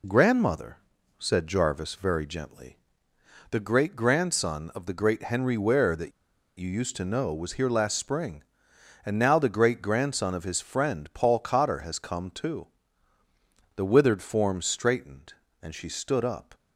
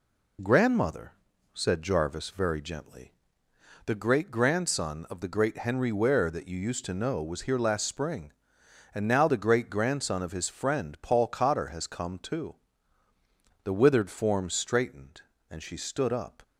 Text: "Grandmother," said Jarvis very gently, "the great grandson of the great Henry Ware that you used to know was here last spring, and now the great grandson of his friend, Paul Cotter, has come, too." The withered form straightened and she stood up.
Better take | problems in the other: second | pauses between "that" and "you"; noticeable; at 6.1 s; 0.47 s long

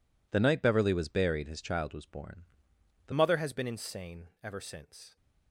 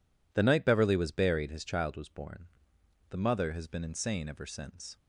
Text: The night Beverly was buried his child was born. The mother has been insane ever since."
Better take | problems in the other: second | changes voice at "mother"; from 3.1 s on; 2.0 s long // pauses between "insane" and "ever"; slight; at 4.2 s; 0.16 s long

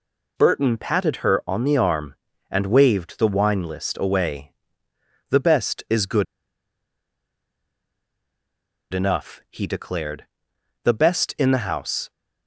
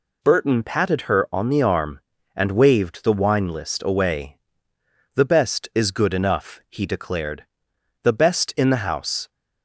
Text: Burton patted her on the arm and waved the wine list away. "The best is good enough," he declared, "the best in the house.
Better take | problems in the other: second | pauses between "good" and "enough"; strong; at 6.2 s; 2.6 s long

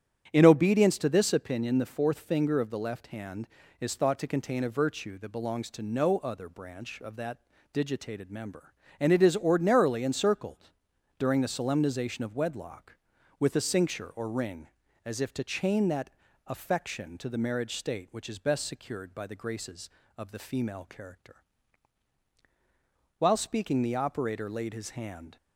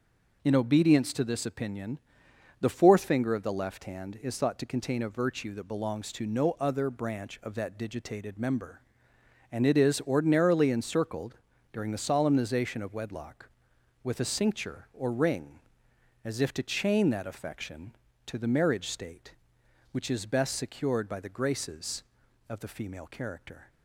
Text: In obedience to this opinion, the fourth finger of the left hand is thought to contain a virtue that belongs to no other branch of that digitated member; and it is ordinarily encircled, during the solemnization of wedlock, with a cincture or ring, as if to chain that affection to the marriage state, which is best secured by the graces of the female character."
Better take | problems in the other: second | starts louder than the rest; strong; until 1.3 s; 8.5 dB // pauses between "that" and "digitated"; slight; at 7.3 s; 0.34 s long // pauses between "that" and "affection"; at 16.1 s; 0.38 s long // goes on to say "While speaking the operator laid his hand"; strong; from 23.1 s on; 2.1 s long

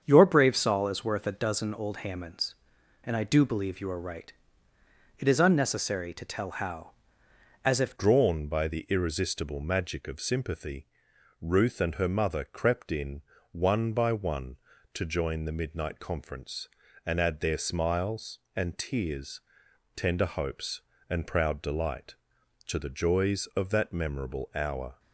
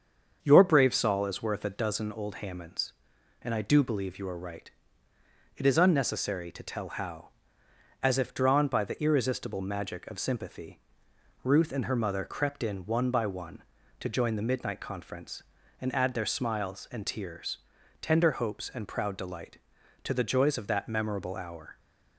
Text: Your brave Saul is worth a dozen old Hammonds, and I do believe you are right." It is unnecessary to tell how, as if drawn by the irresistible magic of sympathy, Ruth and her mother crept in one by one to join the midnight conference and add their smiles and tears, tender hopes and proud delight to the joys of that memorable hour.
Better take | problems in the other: second | starts louder than the rest; strong; until 1.0 s; 7.5 dB; also in the second // changes voice at "drawn"; from 7.9 s on; 17.0 s long // pauses between "in" and "one"; slight; at 13.2 s; 0.30 s long

